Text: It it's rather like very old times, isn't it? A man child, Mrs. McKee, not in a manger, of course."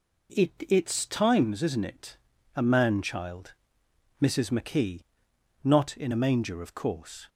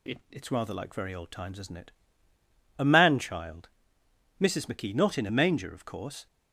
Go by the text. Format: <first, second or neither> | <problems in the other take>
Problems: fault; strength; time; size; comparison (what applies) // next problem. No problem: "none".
second | skips "rather like very old"; at 1.0 s